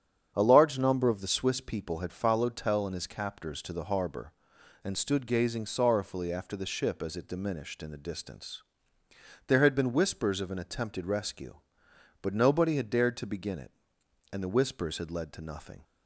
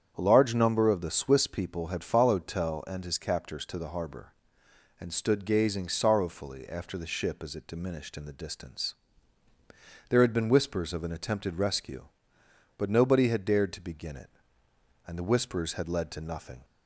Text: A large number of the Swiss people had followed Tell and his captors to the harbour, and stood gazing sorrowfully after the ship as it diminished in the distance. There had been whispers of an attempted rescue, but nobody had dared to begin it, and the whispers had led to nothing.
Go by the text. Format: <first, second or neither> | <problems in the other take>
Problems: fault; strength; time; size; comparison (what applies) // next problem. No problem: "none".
neither | starts louder than the rest; strong; the same in both